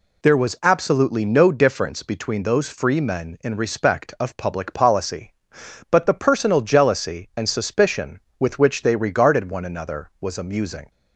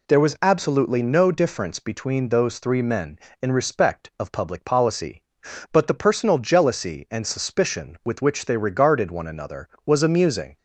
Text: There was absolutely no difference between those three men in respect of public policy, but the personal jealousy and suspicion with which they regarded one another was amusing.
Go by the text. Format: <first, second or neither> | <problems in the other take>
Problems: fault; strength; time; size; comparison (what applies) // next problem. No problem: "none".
second | says "free" for "three"; at 2.6 s